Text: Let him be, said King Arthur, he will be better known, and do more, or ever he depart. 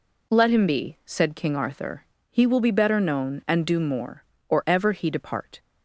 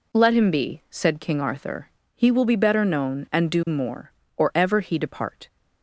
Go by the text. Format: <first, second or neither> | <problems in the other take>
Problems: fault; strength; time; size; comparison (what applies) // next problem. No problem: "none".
neither | none